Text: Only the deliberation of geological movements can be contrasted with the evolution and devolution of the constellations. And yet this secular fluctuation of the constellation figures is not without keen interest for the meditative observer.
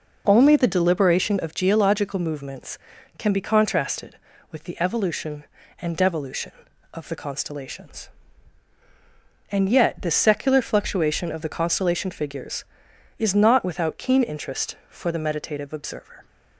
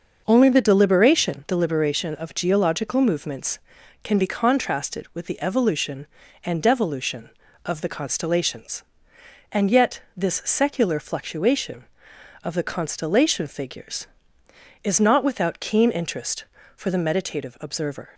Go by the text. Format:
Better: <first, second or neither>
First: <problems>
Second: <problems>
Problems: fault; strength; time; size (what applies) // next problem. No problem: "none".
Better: first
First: none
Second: starts louder than the rest; until 1.2 s; 6.5 dB // says "deliberation" twice; at 1.4 s // pauses between "yet" and "this"; slight; at 9.9 s; 0.16 s long